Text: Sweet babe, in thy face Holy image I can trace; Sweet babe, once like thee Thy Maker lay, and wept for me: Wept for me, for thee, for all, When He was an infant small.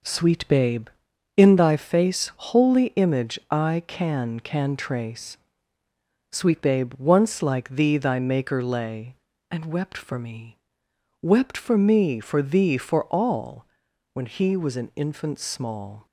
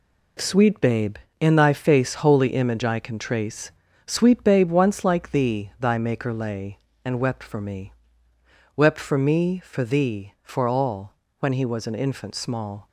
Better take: second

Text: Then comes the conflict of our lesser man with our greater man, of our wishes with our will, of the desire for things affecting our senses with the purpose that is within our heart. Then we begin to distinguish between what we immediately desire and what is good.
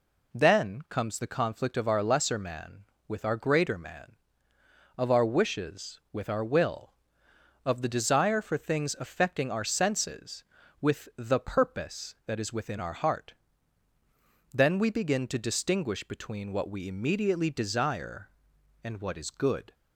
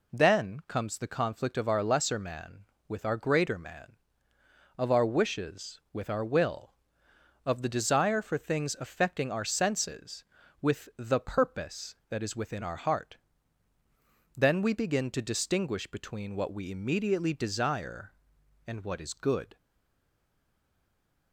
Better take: first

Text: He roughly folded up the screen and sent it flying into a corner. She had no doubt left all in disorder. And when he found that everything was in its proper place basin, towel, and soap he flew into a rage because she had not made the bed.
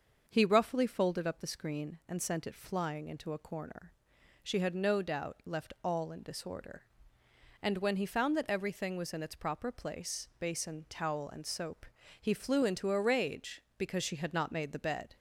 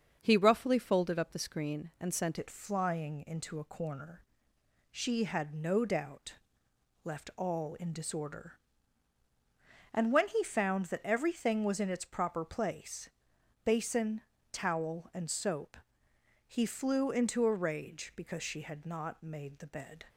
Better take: first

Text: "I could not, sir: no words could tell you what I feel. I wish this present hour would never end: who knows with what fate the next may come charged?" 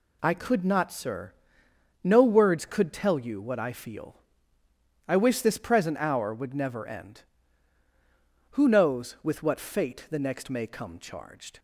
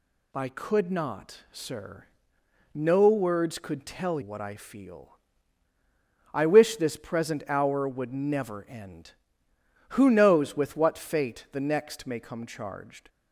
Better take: first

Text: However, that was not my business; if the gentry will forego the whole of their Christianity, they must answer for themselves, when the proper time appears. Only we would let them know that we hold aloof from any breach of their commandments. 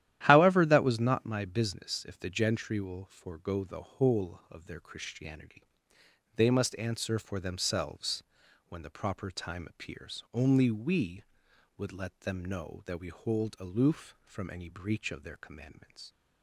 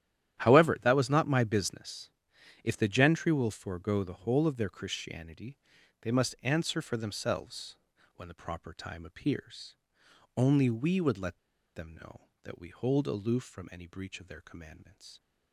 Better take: first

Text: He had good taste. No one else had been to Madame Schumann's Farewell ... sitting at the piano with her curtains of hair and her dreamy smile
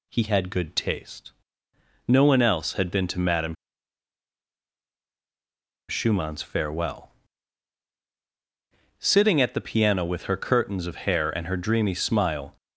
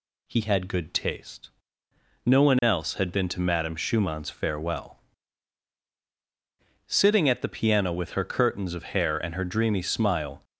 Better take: second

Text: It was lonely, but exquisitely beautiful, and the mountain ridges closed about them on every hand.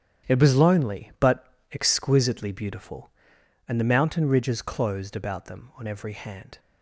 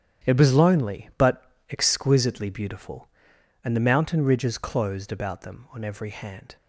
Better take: neither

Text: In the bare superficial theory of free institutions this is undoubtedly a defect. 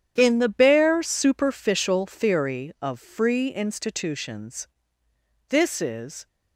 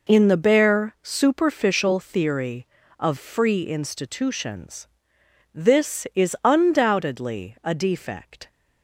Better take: second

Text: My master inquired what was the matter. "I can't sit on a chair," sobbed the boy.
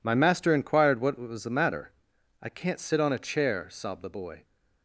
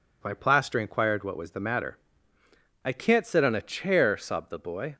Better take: first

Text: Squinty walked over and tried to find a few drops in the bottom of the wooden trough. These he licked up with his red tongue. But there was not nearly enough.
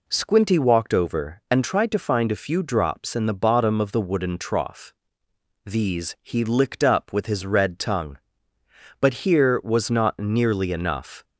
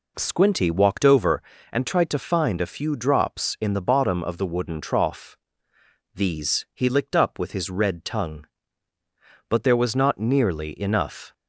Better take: second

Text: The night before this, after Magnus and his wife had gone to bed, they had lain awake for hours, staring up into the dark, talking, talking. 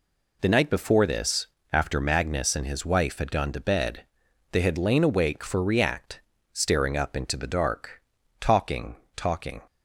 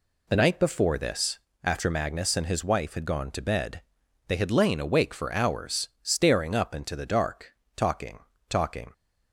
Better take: second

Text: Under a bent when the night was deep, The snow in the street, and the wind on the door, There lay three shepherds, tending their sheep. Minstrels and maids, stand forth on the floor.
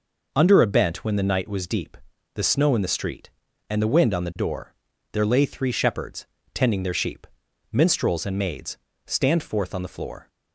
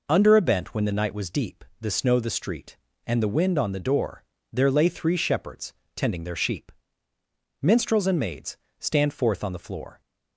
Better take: first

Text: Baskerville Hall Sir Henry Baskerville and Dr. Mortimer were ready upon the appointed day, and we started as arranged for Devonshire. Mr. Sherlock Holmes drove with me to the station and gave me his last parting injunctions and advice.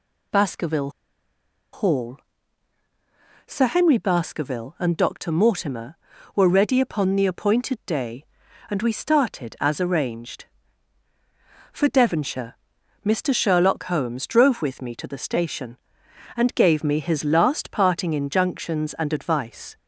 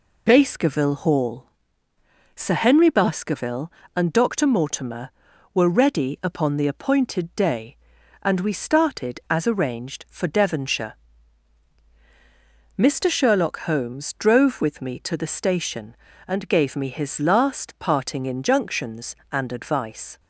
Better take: second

